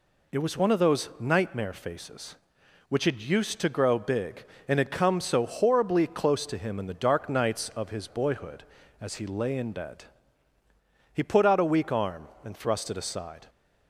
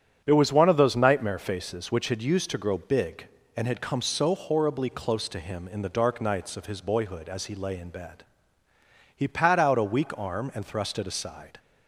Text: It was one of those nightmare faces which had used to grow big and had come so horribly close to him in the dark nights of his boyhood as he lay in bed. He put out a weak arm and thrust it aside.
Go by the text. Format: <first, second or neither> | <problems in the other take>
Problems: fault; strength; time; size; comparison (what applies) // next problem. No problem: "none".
first | starts louder than the rest; strong; until 1.2 s; 8 dB // says "pat" for "put"; at 9.2 s